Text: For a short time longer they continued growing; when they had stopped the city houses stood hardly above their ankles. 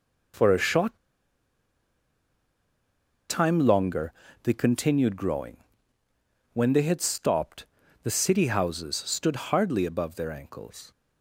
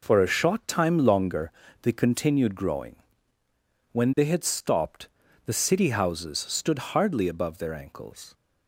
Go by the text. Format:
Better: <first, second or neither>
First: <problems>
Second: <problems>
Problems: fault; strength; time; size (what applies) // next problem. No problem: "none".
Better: second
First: pauses between "short" and "time"; strong; at 0.9 s; 2.3 s long // pauses between "longer" and "they"; slight; at 4.1 s; 0.34 s long // pauses between "stopped" and "the"; slight; at 7.6 s; 0.34 s long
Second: pauses between "longer" and "they"; slight; at 1.4 s; 0.34 s long // pauses between "stopped" and "the"; slight; at 5.0 s; 0.34 s long